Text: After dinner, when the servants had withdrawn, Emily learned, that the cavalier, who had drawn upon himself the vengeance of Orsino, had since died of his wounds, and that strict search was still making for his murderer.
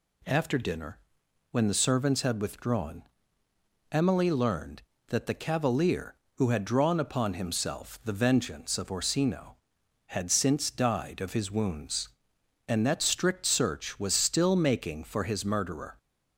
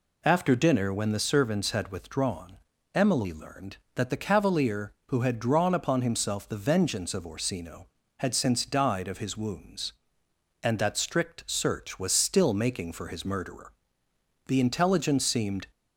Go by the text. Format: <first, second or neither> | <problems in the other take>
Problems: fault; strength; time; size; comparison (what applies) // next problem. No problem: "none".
first | goes on to say "The intelligence seemed"; noticeable; from 14.4 s on; 1.2 s long